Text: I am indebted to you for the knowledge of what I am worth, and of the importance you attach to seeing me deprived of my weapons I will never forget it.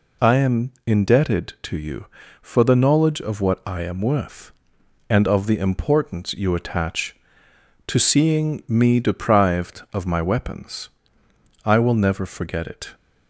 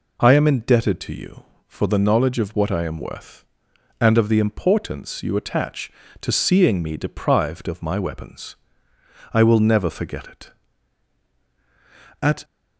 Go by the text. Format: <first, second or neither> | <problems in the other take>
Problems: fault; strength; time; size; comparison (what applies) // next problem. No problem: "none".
first | pauses between "weapons" and "I"; noticeable; at 8.5 s; 0.80 s long; noticeable in the first // goes on to say "At"; slight; from 12.2 s on; 0.22 s long